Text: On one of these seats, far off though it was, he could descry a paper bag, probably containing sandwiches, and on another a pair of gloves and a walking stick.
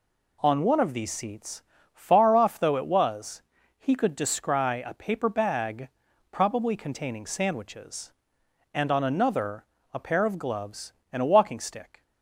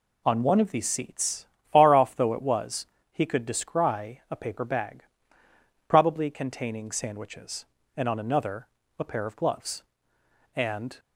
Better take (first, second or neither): first